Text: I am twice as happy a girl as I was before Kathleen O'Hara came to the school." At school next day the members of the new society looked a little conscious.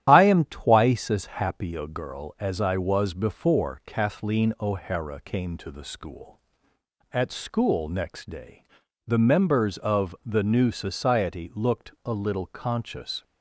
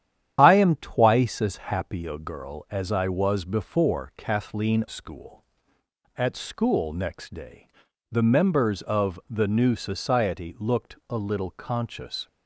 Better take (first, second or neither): first